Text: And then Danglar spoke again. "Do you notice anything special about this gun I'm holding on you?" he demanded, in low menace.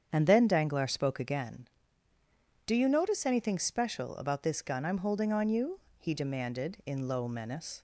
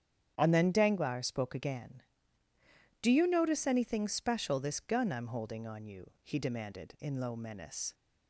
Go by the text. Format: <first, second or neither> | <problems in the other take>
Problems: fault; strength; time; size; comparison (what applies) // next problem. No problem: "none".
first | starts louder than the rest; strong; until 1.3 s; 9 dB; strong in the first // skips "about"; at 4.5 s